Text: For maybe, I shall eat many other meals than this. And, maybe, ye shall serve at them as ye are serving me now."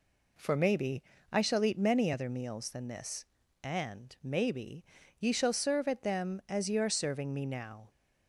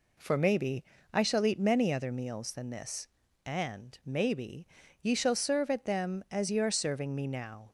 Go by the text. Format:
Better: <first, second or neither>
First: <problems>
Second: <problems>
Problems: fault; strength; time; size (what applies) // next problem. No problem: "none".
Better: neither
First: none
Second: none